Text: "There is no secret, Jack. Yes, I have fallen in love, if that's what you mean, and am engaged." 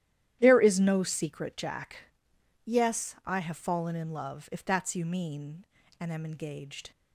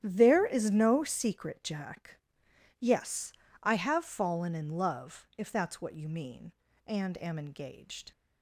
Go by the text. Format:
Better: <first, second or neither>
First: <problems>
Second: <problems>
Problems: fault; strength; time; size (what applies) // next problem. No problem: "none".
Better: second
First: starts louder than the rest; strong; until 1.4 s; 12 dB // skips "what"; at 4.9 s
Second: starts louder than the rest; strong; until 1.0 s; 11 dB